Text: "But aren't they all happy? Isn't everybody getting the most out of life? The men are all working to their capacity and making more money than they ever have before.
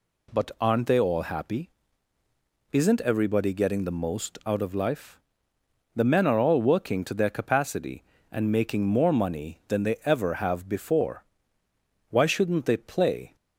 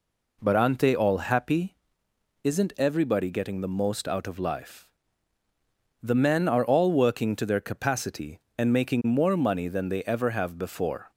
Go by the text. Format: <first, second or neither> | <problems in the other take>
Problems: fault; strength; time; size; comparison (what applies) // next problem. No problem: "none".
second | goes on to say "Why shouldn't they play"; noticeable; from 12.0 s on; 1.2 s long